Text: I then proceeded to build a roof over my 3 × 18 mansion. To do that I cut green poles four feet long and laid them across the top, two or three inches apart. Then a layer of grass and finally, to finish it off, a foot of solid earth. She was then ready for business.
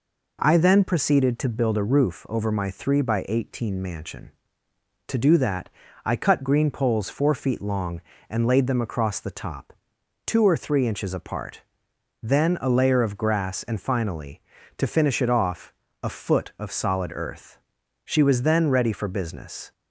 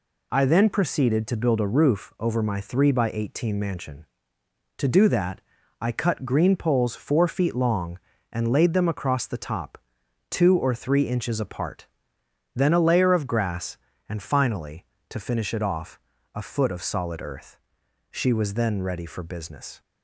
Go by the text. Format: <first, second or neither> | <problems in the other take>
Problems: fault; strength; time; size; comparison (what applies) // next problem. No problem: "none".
neither | pauses between "that" and "I"; the same in both